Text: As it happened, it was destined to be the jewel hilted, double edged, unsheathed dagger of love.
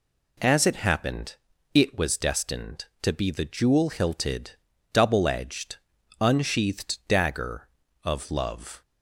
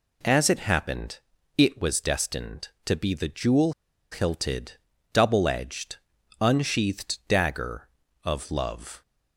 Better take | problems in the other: first | pauses between "jewel" and "hilted"; at 3.7 s; 0.40 s long

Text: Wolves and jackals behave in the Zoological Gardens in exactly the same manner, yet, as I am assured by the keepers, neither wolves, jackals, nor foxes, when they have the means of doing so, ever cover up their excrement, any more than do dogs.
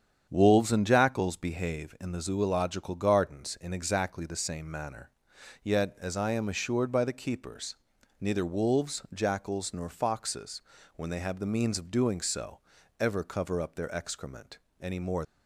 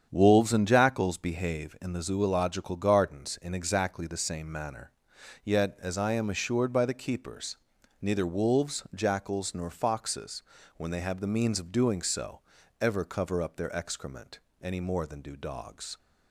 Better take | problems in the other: second | starts louder than the rest; strong; until 1.3 s; 8 dB; strong in the second // stops before "than do dogs"; at 15.2 s

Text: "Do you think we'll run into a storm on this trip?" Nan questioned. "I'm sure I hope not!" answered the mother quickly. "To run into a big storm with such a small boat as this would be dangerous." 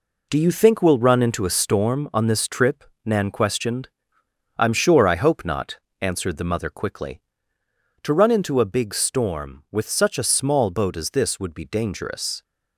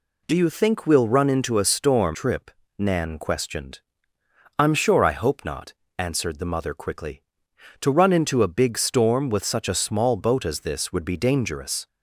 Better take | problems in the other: first | skips "on this"; at 2.1 s

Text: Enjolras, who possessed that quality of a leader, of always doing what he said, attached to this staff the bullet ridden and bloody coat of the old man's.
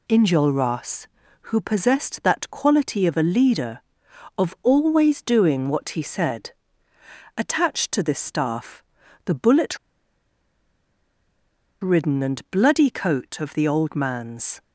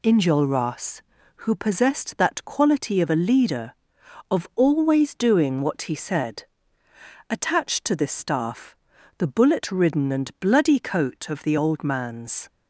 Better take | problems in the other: second | pauses between "staff" and "the"; at 8.8 s; 0.42 s long; also in the second // pauses between "bullet" and "ridden"; strong; at 9.7 s; 2.0 s long

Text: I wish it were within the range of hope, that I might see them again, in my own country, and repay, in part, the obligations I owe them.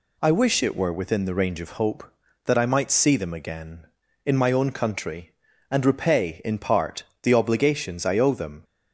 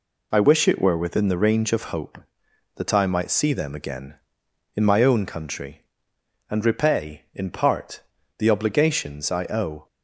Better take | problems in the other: first | stops before "them"; at 9.8 s

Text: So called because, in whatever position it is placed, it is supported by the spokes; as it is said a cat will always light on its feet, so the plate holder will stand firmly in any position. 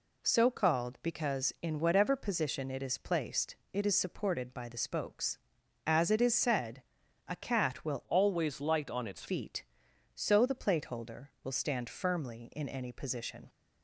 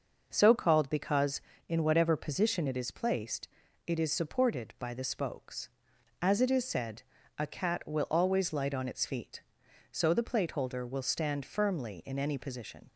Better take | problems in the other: second | pauses between "said" and "a"; at 6.8 s; 0.44 s long; slight in the second // changes voice from "always" to "its"; from 8.0 to 9.2 s; 1.2 s long

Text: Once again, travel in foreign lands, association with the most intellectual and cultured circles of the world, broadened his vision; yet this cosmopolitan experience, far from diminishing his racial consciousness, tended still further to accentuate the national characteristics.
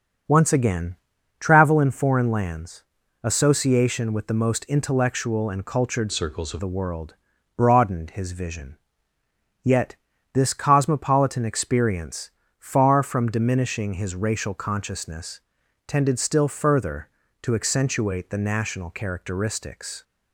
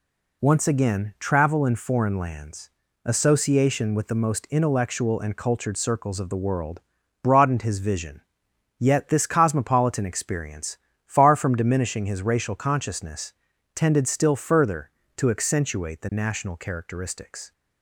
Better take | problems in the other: second | starts louder than the rest; noticeable; until 1.7 s; 6 dB // changes voice from "circles" to "of"; from 6.1 to 6.5 s; 0.4 s long // pauses between "yet" and "this"; at 9.9 s; 0.38 s long

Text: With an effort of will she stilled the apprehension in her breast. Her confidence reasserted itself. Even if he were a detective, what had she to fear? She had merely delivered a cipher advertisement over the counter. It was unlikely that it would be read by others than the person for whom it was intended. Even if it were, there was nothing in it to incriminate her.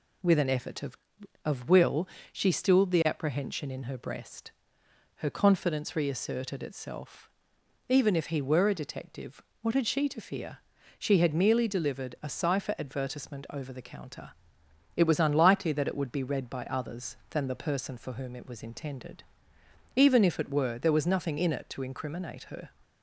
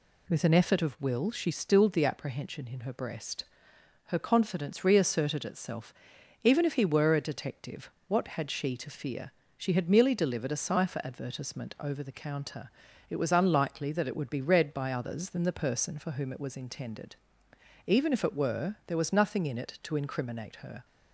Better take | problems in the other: second | says "of" twice; at 1.4 s // pauses between "will" and "she"; slight; at 2.0 s; 0.24 s long

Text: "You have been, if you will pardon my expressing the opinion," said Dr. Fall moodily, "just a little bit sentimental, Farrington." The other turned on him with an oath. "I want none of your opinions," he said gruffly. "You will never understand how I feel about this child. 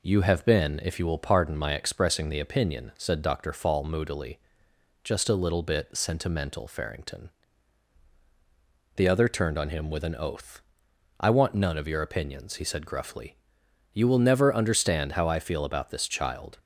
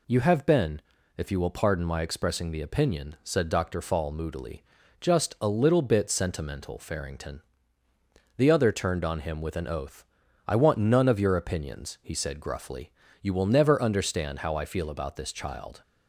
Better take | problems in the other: neither | none

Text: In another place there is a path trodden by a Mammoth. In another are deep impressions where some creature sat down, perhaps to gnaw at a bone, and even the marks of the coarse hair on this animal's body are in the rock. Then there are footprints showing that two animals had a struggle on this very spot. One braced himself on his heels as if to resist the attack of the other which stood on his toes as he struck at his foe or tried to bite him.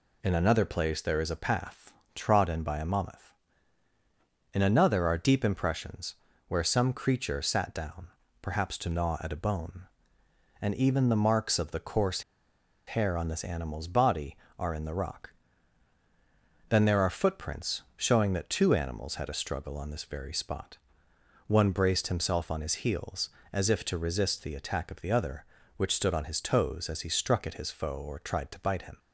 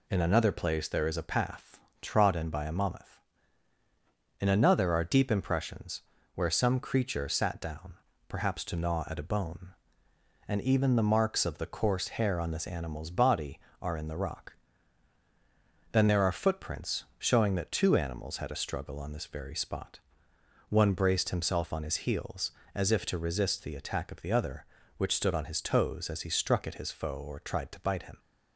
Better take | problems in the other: second | pauses between "path" and "trodden"; slight; at 1.9 s; 0.22 s long; slight in the second // pauses between "impressions" and "where"; slight; at 6.1 s; 0.34 s long; slight in the second // pauses between "coarse" and "hair"; noticeable; at 12.2 s; 0.66 s long

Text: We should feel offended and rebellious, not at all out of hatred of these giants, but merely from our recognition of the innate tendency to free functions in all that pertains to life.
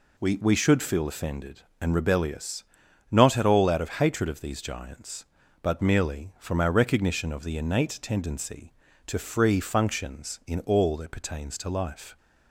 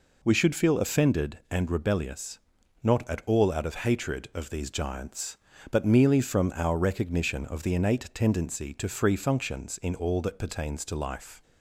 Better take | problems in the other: second | says "We" twice; at 0.4 s

